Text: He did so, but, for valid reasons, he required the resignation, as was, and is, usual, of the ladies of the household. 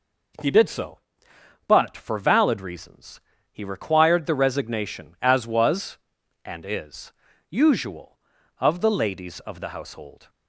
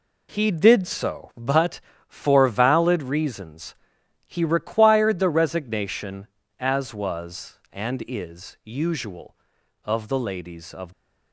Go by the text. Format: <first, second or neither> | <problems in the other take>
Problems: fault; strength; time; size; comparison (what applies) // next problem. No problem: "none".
first | stops before "the household"; at 10.9 s